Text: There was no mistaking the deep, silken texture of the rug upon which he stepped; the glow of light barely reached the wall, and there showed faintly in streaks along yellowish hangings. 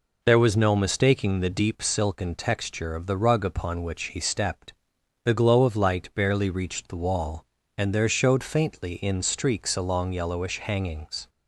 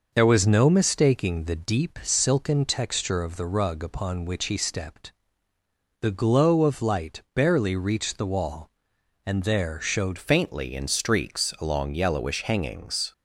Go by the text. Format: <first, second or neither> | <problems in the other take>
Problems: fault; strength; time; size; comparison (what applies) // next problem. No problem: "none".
first | changes voice at "faintly"; from 10.1 s on; 3.0 s long